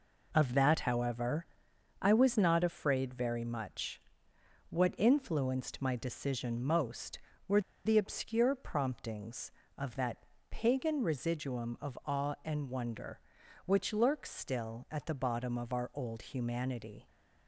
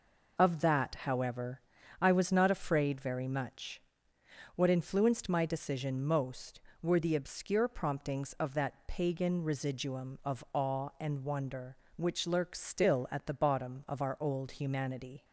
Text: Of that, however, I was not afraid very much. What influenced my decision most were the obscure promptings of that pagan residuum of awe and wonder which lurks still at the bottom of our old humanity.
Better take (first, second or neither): second